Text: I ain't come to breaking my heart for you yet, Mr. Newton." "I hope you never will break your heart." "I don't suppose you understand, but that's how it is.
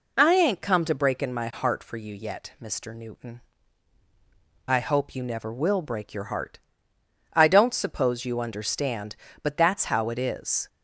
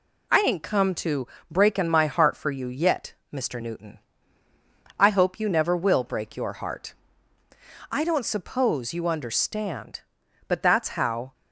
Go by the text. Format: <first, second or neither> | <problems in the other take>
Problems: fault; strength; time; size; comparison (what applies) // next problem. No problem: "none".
first | pauses between "to" and "breaking"; slight; at 1.2 s; 0.24 s long // stops before "it is"; at 11.3 s